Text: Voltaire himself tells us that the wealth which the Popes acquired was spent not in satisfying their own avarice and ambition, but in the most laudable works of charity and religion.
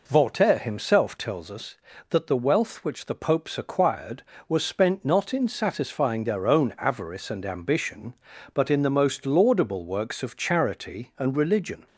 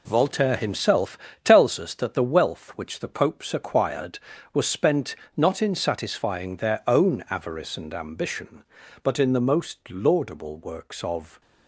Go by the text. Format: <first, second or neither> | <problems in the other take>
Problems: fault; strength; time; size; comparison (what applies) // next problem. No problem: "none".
first | pauses between "himself" and "tells"; slight; at 1.1 s; 0.24 s long // pauses between "spent" and "not"; slight; at 5.1 s; 0.20 s long // stops before "charity and religion"; at 11.4 s